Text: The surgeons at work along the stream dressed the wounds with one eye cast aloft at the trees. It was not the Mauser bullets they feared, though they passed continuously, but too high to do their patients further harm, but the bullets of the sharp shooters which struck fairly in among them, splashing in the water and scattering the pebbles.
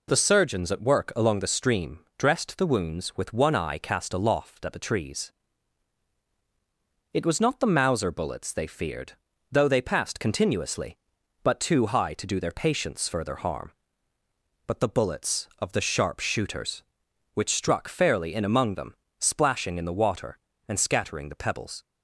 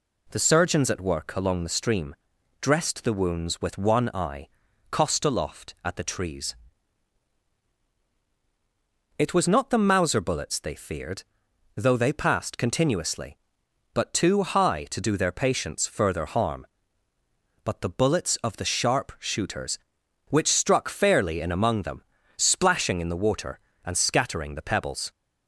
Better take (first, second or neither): first